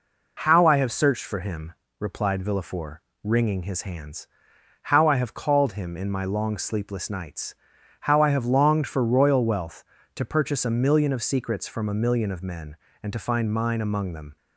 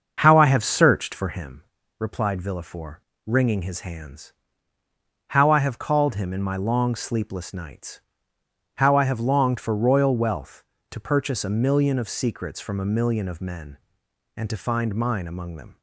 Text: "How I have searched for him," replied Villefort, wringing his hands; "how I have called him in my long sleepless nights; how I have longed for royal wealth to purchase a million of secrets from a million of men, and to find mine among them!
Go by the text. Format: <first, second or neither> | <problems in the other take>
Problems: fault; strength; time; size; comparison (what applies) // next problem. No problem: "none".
first | starts louder than the rest; until 1.6 s; 6.5 dB